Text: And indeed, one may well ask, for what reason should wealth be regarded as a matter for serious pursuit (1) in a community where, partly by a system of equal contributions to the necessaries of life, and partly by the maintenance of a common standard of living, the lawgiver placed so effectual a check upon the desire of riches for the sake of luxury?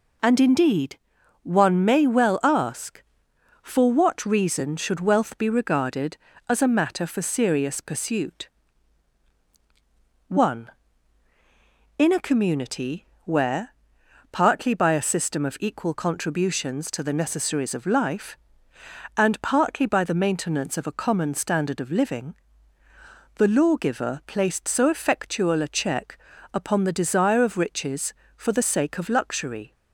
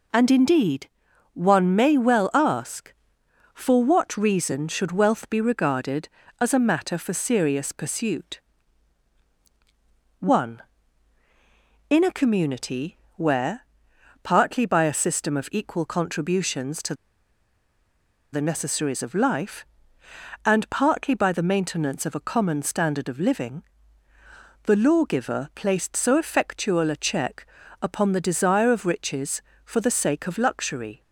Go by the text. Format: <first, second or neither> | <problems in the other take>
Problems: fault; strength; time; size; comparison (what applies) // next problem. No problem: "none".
first | pauses between "community" and "where"; slight; at 12.9 s; 0.20 s long; slight in the first // pauses between "to" and "the"; strong; at 16.9 s; 1.3 s long // pauses between "check" and "upon"; slight; at 27.4 s; 0.36 s long; slight in the first